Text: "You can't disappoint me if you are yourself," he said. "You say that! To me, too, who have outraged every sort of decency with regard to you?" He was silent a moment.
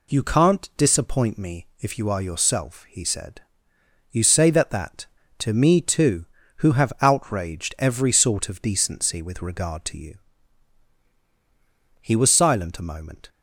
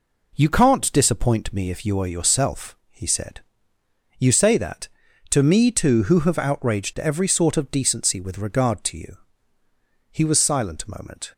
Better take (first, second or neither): second